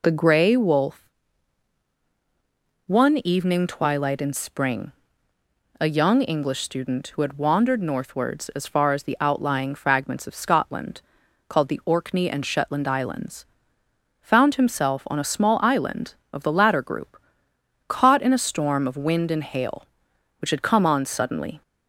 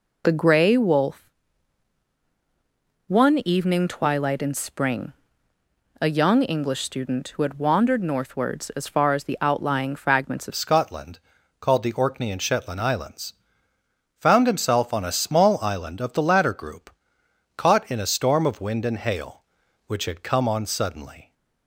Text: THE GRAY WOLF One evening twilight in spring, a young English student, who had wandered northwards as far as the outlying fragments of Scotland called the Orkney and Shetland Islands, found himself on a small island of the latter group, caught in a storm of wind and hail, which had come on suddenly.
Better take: first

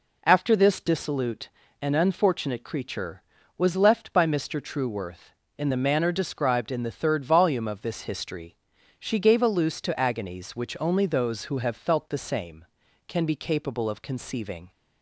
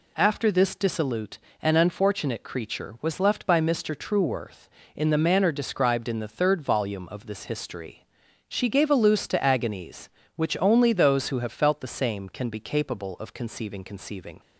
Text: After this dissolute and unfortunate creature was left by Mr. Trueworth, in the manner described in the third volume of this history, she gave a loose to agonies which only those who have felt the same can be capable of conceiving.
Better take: first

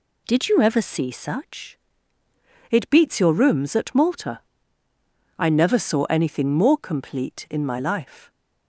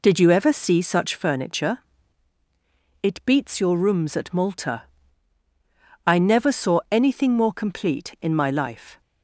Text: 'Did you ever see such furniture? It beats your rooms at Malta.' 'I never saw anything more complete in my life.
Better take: second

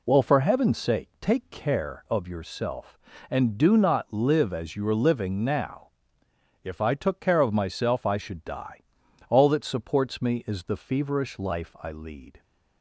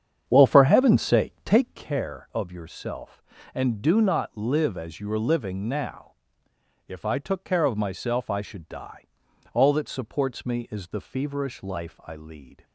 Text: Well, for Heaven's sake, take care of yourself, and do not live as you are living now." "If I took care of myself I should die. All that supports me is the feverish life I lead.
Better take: first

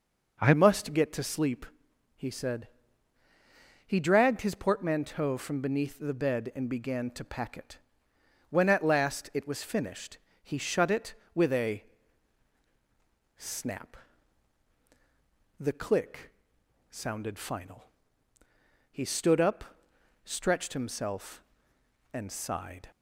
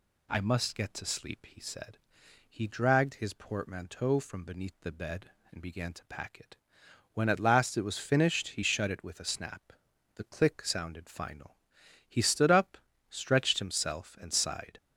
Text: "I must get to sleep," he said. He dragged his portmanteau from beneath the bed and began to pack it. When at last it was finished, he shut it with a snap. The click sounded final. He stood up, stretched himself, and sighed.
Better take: second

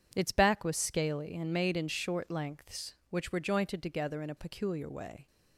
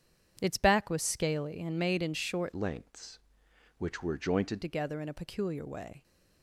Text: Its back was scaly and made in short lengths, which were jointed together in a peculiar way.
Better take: first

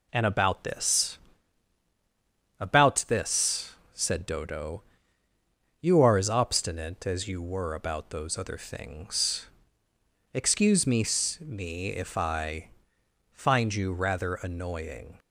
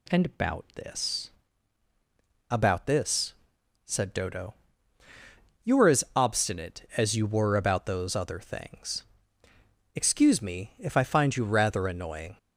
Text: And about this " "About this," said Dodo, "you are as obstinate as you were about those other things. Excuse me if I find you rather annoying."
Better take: second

